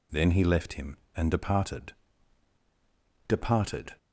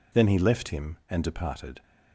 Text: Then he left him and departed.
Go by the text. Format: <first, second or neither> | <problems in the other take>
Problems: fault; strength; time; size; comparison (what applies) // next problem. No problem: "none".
second | says "departed" twice; at 3.2 s